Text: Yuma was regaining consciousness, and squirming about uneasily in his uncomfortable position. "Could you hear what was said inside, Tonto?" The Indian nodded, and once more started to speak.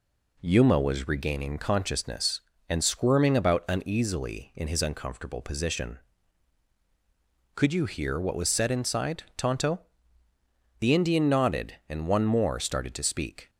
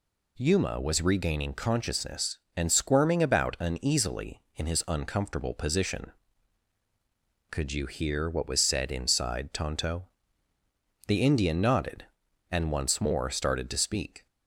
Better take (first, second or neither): second